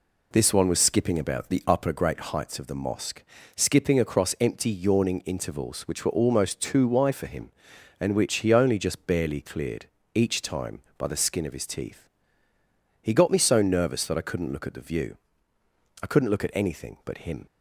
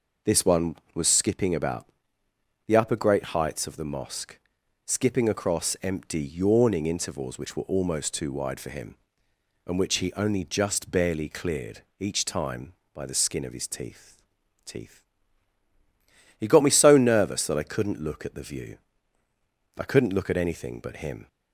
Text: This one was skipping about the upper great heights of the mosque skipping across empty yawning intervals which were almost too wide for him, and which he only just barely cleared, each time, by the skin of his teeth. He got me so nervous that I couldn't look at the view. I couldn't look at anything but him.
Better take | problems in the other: first | pauses between "about" and "the"; noticeable; at 1.8 s; 0.82 s long // pauses between "mosque" and "skipping"; noticeable; at 4.3 s; 0.47 s long; slight in the first // says "teeth" twice; at 14.6 s

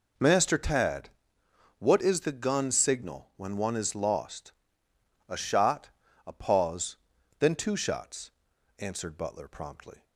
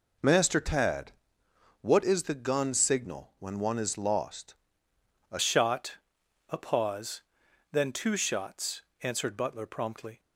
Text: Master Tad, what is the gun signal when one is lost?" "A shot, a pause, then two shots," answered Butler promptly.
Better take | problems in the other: first | changes voice at "shot"; from 5.3 s on; 4.8 s long

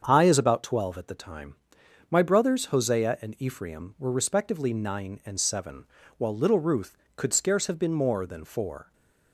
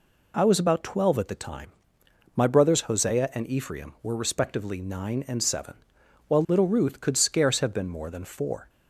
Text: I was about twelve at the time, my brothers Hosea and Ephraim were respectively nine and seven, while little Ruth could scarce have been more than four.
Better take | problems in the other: second | starts louder than the rest; strong; until 1.0 s; 7 dB // says "is" for "was"; at 0.2 s

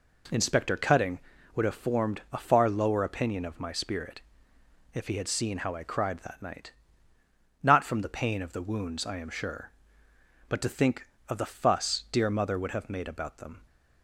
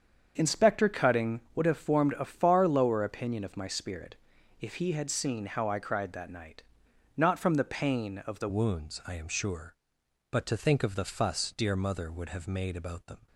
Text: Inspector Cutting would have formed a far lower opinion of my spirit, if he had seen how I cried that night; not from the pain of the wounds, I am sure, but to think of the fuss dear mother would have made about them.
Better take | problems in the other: first | starts louder than the rest; strong; until 1.5 s; 7.5 dB // changes voice at "wounds"; from 8.4 s on; 4.8 s long

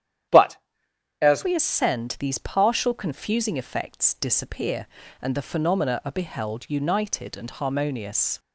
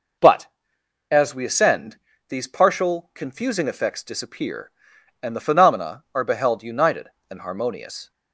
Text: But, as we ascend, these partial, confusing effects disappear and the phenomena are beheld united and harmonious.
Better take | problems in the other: second | starts louder than the rest; strong; until 1.9 s; 10.5 dB // changes voice at "we"; from 1.4 s on; 6.9 s long

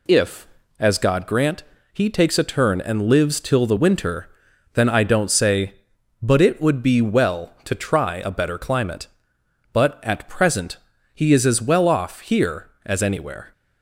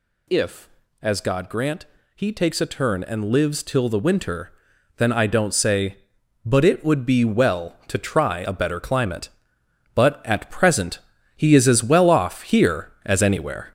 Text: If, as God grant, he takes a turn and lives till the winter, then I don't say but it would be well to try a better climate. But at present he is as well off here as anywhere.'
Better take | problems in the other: first | gets louder; noticeable; throughout; 4.5 dB // pauses between "present" and "he"; slight; at 10.9 s; 0.36 s long; slight in the first

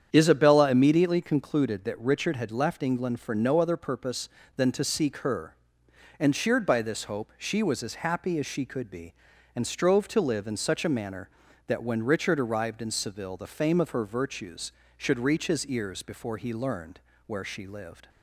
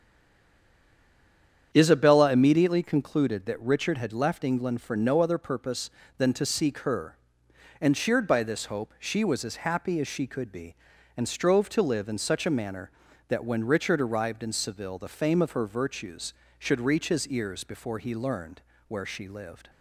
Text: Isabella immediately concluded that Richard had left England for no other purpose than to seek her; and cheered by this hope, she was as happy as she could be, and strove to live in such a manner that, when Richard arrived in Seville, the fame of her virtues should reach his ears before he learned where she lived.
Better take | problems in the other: first | stays silent before the first word; noticeable; until 1.7 s; 1.7 s long // starts louder than the rest; strong; until 2.7 s; 8.5 dB; strong in the first // pauses between "learned" and "where"; slight; at 18.5 s; 0.28 s long; slight in the first

